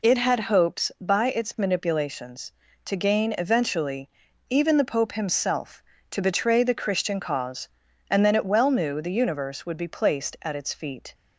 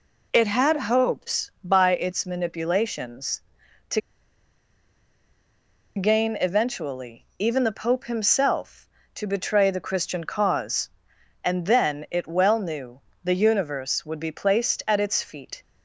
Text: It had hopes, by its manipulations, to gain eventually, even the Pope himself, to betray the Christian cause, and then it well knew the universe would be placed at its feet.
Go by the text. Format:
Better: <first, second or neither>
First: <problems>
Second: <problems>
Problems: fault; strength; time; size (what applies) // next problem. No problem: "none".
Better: first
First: none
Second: pauses between "to" and "gain"; strong; at 4.0 s; 1.9 s long // pauses between "knew" and "the"; slight; at 13.0 s; 0.22 s long